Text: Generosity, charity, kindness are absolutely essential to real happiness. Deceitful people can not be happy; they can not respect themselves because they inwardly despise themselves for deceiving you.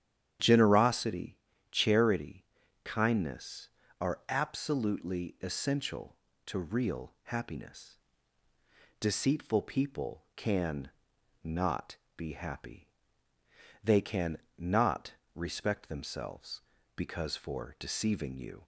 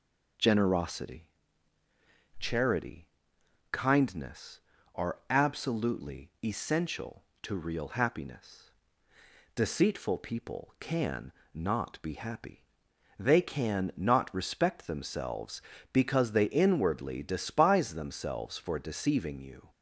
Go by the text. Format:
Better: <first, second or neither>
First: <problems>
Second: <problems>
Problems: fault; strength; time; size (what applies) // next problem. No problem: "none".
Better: second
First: starts louder than the rest; strong; until 1.7 s; 9.5 dB // pauses between "can" and "not"; noticeable; at 10.8 s; 0.54 s long // pauses between "not" and "be"; slight; at 11.9 s; 0.20 s long // pauses between "can" and "not"; slight; at 14.3 s; 0.18 s long // pauses between "not" and "respect"; slight; at 15.1 s; 0.24 s long // skips "they inwardly despise themselves"; at 17.3 s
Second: pauses between "can" and "not"; slight; at 11.3 s; 0.22 s long